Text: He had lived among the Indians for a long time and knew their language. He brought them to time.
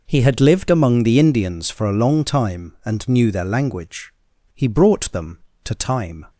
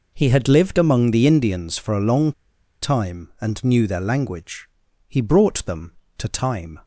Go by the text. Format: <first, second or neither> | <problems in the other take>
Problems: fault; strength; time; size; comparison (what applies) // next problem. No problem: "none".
first | pauses between "long" and "time"; noticeable; at 2.3 s; 0.50 s long